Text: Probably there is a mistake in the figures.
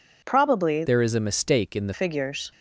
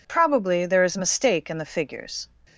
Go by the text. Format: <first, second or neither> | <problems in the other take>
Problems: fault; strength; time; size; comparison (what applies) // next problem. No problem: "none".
second | changes voice from "there" to "the"; from 0.8 to 1.9 s; 1.1 s long